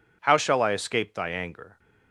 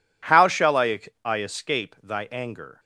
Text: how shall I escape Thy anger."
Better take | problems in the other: first | says "I" twice; at 1.2 s

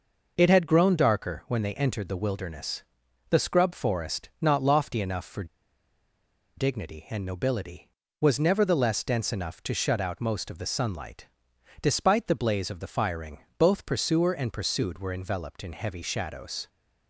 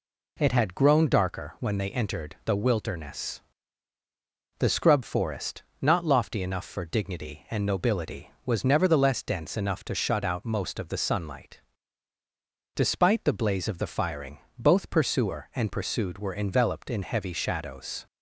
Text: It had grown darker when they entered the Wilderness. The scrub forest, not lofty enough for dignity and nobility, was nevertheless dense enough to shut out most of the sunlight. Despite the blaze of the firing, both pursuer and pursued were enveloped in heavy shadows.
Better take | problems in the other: second | pauses between "for" and "dignity"; at 5.4 s; 1.1 s long

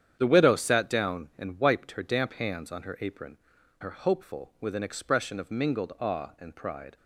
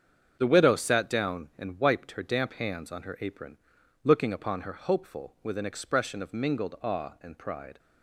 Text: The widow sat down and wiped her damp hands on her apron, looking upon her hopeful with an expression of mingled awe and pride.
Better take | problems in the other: second | starts louder than the rest; strong; until 1.2 s; 9 dB; strong in the second // skips "looking upon"; at 3.5 s

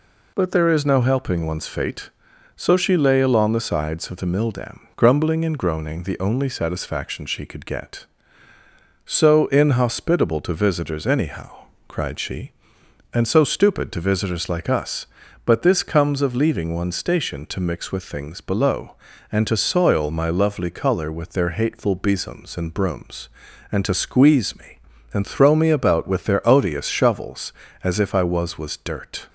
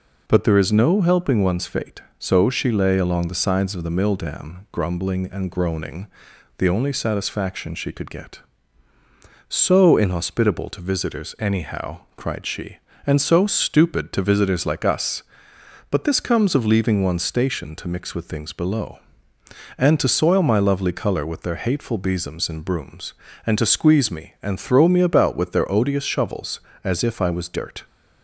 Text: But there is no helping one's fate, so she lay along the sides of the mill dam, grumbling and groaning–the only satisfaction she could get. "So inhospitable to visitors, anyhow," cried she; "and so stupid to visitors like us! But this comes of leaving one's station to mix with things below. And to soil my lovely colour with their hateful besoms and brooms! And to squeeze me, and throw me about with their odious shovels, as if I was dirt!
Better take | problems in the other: second | says "was" twice; at 28.5 s

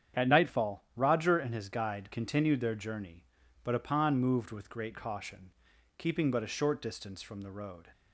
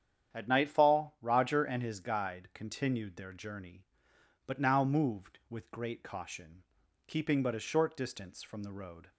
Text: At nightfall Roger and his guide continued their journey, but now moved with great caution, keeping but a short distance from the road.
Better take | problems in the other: second | starts louder than the rest; strong; until 1.2 s; 8.5 dB; strong in the second // says "upon" for "now"; at 3.7 s

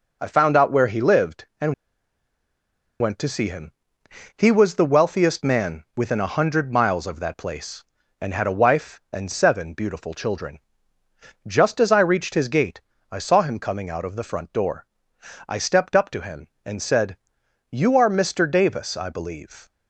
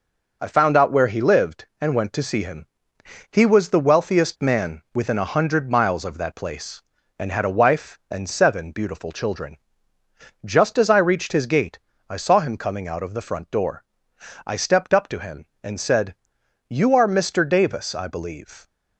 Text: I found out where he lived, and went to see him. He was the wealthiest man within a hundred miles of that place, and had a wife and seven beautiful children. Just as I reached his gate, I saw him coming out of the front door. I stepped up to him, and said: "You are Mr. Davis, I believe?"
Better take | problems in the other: second | pauses between "and" and "went"; strong; at 1.7 s; 1.2 s long

